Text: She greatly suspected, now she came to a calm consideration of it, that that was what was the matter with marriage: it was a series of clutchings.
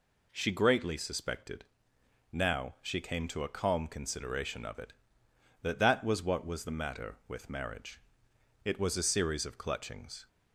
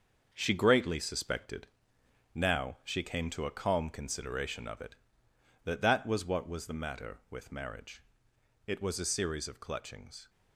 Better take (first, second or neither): first